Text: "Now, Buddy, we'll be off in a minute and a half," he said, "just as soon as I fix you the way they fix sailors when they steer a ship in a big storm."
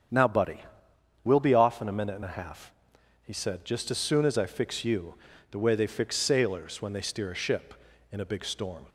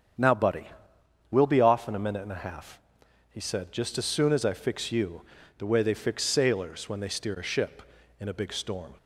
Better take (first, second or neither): neither